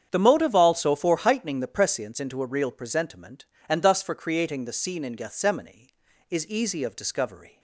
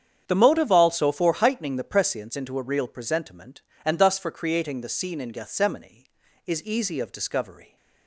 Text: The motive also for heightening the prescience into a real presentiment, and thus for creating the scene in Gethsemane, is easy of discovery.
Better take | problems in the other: neither | starts louder than the rest; strong; the same in both

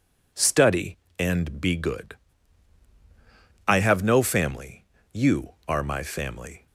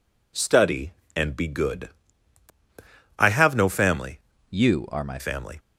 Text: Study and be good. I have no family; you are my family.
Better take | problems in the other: first | changes voice from "you" to "my"; from 4.4 to 5.1 s; 0.7 s long

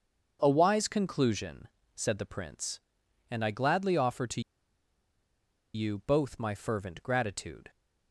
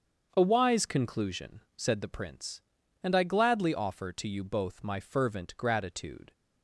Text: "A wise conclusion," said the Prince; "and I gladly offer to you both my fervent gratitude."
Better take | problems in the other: second | starts louder than the rest; until 1.4 s; 6.5 dB; also in the second // pauses between "to" and "you"; strong; at 4.4 s; 1.3 s long

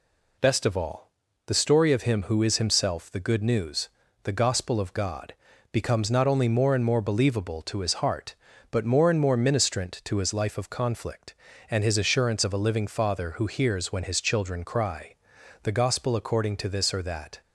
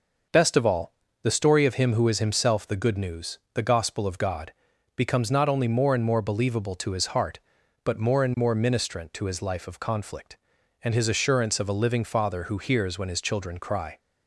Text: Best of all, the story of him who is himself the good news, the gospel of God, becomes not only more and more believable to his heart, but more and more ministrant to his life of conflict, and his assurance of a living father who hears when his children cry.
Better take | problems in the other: second | goes on to say "The gospel according to this or that"; strong; from 15.6 s on; 1.7 s long

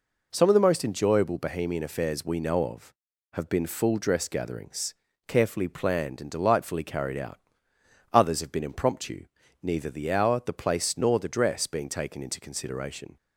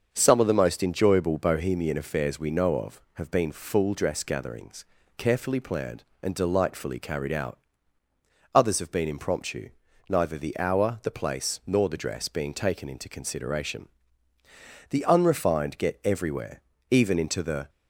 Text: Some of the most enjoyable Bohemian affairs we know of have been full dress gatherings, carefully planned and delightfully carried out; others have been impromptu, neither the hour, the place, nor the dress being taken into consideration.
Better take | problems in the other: first | starts louder than the rest; until 1.1 s; 6.5 dB // goes on to say "The unrefined get everywhere even into the"; strong; from 14.8 s on; 2.8 s long

